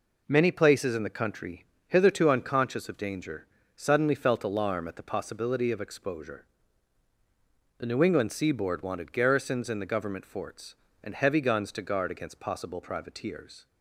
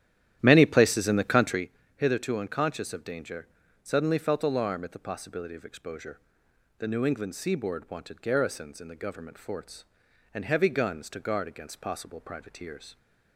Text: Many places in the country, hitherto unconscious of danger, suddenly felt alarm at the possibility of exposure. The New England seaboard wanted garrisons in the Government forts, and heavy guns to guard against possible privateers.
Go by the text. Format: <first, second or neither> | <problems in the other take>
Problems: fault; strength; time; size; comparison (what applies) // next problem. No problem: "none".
first | starts louder than the rest; strong; until 1.7 s; 11.5 dB